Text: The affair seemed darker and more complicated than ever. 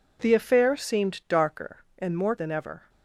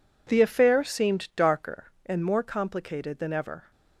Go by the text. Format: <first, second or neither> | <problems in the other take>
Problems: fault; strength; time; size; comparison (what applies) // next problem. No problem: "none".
second | skips "complicated"; at 2.3 s